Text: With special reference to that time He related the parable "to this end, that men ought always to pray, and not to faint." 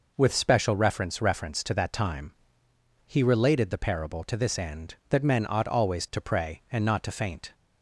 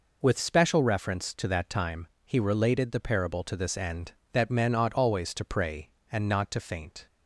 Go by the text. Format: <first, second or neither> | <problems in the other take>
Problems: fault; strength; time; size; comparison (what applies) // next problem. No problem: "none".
second | says "reference" twice; at 1.1 s // pauses between "time" and "He"; noticeable; at 2.3 s; 0.70 s long; slight in the second